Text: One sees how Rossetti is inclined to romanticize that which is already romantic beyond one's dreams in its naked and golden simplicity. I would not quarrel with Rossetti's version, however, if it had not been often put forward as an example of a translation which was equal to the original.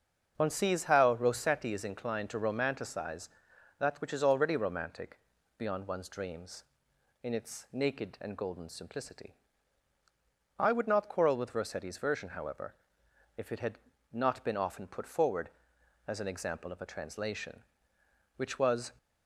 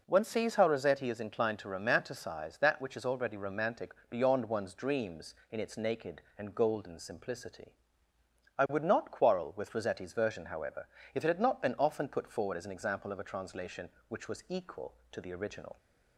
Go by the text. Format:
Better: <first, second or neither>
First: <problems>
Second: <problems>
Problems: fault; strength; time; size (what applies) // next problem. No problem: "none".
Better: second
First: starts louder than the rest; strong; until 1.3 s; 7 dB // pauses between "romantic" and "beyond"; at 5.1 s; 0.38 s long // pauses between "had" and "not"; slight; at 13.7 s; 0.32 s long // stops before "equal to the original"; at 18.9 s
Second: pauses between "romantic" and "beyond"; slight; at 3.9 s; 0.16 s long